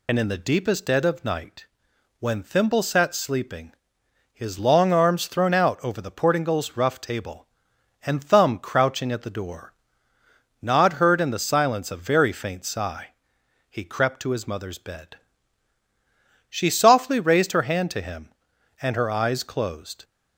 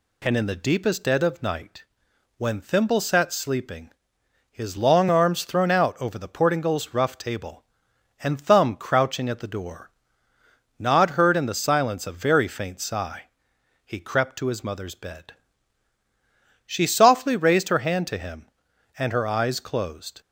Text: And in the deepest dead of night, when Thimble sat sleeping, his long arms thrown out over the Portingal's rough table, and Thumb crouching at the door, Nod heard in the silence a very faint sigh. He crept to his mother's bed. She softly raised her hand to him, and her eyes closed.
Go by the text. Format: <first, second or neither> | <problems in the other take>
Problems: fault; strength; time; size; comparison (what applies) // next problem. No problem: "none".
second | loses the start of "And"; at 0.0 s; 50 ms